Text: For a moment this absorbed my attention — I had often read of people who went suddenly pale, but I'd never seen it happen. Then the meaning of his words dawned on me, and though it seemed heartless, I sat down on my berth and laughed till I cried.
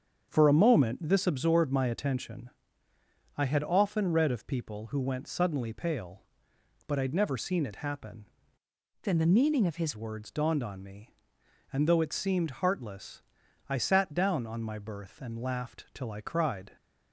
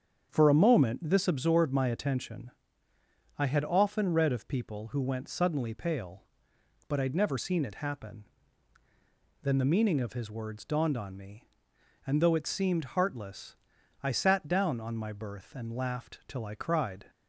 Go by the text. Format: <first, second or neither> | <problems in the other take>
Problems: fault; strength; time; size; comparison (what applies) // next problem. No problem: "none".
second | starts louder than the rest; until 1.3 s; 7 dB; strong in the second // changes voice from "Then" to "his"; from 9.0 to 9.9 s; 0.9 s long